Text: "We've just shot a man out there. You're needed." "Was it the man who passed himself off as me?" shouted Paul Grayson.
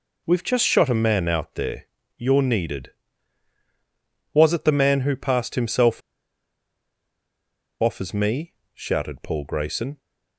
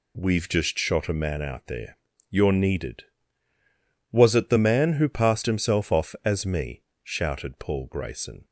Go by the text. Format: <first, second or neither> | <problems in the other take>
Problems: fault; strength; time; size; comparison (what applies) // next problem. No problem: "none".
second | pauses between "himself" and "off"; strong; at 5.9 s; 1.8 s long